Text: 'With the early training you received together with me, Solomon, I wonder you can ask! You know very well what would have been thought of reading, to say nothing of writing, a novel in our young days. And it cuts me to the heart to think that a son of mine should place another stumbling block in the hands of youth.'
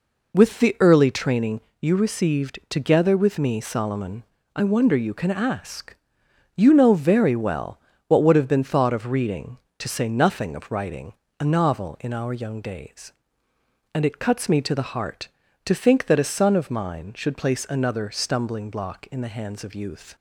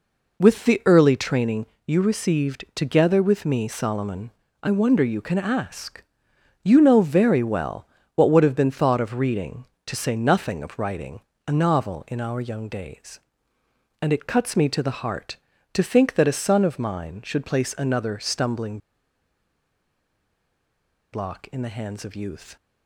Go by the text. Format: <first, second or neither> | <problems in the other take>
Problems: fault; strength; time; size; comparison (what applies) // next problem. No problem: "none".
first | pauses between "training" and "you"; slight; at 1.6 s; 0.18 s long; slight in the first // pauses between "well" and "what"; slight; at 7.8 s; 0.30 s long; slight in the first // pauses between "stumbling" and "block"; strong; at 18.7 s; 2.3 s long